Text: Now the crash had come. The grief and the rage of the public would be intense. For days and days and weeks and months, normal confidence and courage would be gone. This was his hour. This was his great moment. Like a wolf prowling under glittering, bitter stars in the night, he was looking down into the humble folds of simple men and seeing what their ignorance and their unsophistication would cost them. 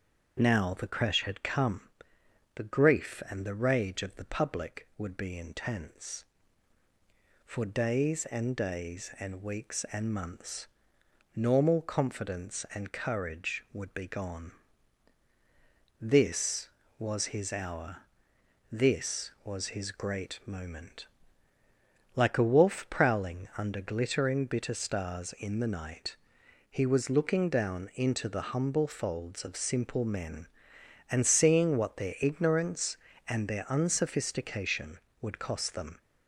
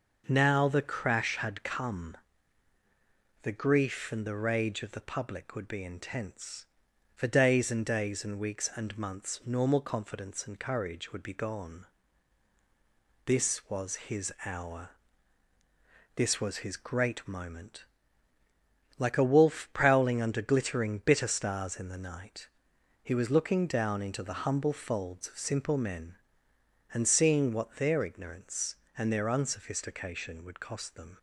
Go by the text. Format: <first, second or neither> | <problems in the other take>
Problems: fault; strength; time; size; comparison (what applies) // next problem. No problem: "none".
neither | starts louder than the rest; the same in both